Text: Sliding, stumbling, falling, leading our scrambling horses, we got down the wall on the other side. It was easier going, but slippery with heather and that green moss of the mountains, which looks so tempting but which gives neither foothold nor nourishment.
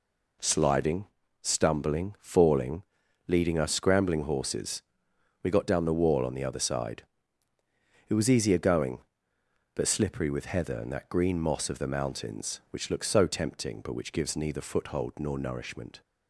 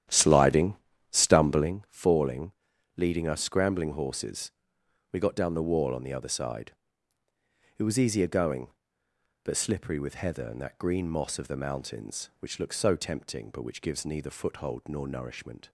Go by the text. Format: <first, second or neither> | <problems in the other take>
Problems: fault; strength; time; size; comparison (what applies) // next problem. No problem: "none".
first | starts louder than the rest; strong; until 1.8 s; 10.5 dB